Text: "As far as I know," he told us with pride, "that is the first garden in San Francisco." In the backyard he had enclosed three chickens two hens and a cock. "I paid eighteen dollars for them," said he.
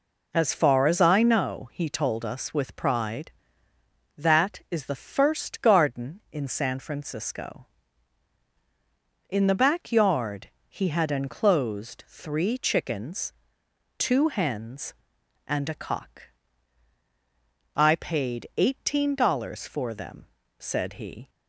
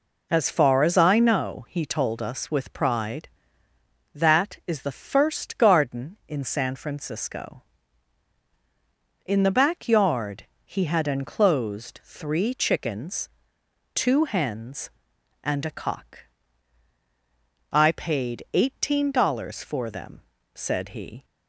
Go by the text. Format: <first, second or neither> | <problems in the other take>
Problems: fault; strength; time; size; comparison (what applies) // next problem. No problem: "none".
neither | pauses between "backyard" and "he"; slight; the same in both // pauses between "chickens" and "two"; noticeable; the same in both